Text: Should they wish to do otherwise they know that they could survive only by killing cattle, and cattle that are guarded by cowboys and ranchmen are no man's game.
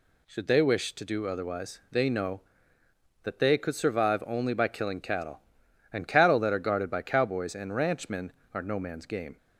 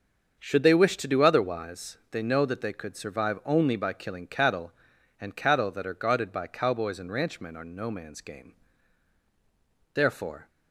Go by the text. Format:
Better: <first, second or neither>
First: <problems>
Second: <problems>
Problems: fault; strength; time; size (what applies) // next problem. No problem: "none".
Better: first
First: none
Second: starts louder than the rest; until 1.4 s; 6.5 dB // goes on to say "Therefore"; from 9.9 s on; 0.54 s long